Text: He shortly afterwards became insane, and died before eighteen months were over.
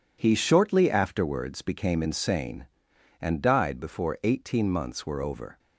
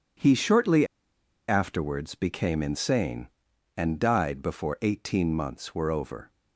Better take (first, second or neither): first